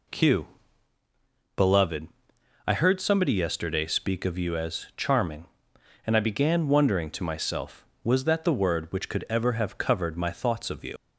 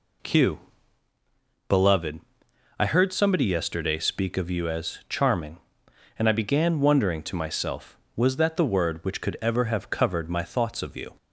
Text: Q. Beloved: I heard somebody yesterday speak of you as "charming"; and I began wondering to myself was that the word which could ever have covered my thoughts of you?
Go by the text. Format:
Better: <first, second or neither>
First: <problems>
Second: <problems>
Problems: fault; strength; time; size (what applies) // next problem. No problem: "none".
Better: second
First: leaves "you" unfinished; at 10.9 s; 85 ms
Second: none